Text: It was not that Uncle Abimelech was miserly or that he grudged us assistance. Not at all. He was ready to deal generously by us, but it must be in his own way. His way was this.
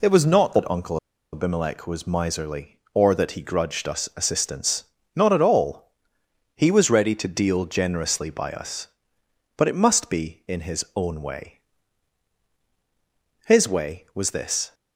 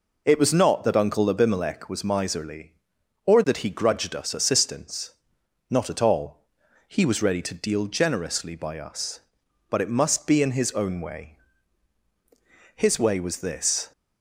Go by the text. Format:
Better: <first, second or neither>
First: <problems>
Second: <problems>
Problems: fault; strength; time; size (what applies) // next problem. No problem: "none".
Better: second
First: pauses between "Uncle" and "Abimelech"; at 0.9 s; 0.36 s long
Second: none